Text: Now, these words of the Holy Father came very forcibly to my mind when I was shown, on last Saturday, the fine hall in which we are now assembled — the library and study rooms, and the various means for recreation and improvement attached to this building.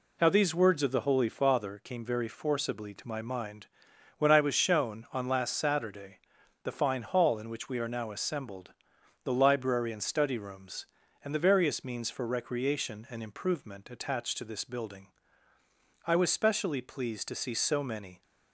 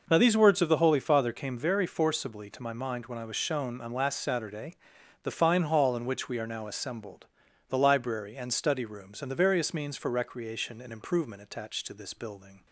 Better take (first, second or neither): second